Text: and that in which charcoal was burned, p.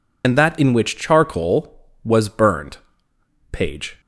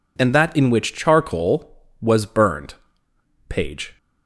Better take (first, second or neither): second